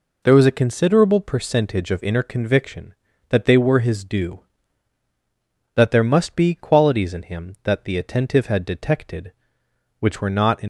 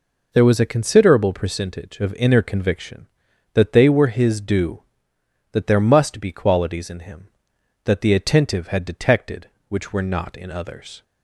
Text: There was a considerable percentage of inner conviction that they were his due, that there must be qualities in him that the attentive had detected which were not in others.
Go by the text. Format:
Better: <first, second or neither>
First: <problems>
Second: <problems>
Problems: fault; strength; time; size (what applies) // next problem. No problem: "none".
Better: second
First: stops before "others"; at 10.6 s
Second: none